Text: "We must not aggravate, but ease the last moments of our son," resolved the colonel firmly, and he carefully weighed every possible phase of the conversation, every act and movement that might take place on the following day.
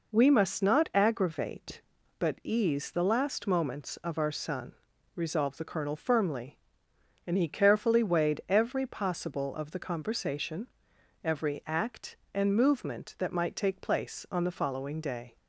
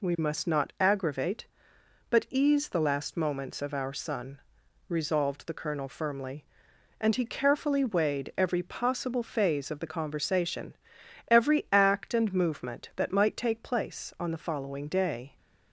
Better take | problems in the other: second | skips "phase"; at 9.5 s

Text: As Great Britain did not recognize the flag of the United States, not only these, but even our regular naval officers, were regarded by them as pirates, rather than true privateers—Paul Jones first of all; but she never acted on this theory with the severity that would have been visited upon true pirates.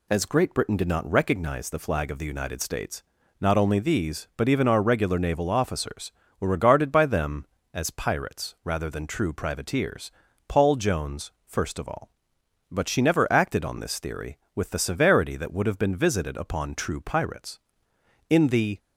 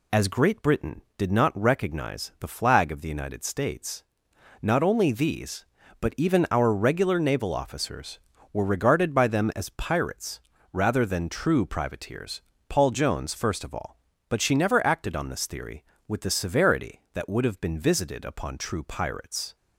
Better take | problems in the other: second | goes on to say "In the"; slight; from 18.3 s on; 0.48 s long

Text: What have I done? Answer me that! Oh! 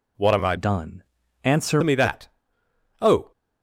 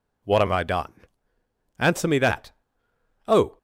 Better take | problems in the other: second | changes voice from "done" to "Answer"; from 0.5 to 1.8 s; 1.3 s long

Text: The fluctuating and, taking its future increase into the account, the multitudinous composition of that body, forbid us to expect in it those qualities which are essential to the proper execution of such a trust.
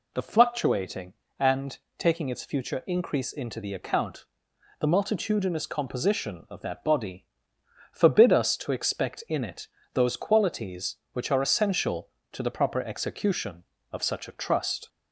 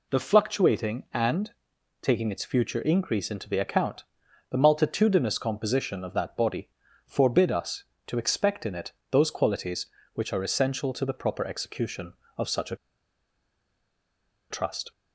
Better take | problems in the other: first | pauses between "it" and "those"; slight; at 8.9 s; 0.18 s long; slight in the first // pauses between "a" and "trust"; strong; at 12.7 s; 1.7 s long

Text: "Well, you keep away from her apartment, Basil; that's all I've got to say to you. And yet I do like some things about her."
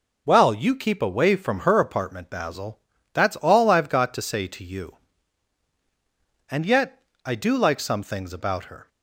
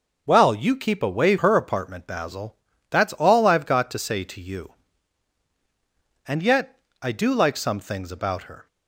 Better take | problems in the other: first | skips "from"; at 1.3 s // pauses between "yet" and "I"; slight; at 6.7 s; 0.22 s long; slight in the first

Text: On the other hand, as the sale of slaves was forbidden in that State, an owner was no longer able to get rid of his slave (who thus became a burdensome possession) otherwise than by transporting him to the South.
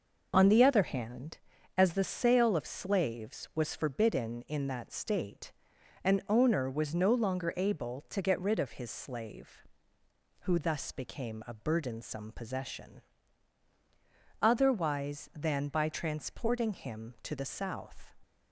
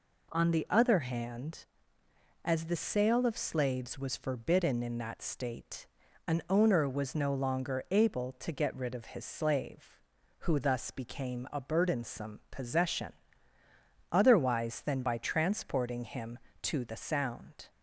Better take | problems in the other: first | says "Sound" for "South"; at 16.9 s

